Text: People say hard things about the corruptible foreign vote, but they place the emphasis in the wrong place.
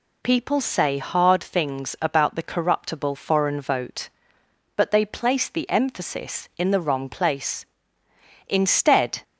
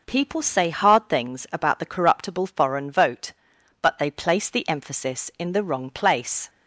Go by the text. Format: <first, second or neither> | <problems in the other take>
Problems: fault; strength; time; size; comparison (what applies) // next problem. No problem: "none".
second | goes on to say "Instead"; noticeable; from 8.4 s on; 0.76 s long